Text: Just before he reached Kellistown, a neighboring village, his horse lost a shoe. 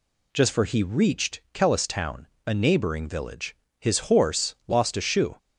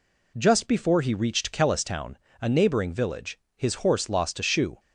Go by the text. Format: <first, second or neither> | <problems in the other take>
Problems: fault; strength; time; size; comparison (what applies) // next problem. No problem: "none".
second | says "for" for "before"; at 0.5 s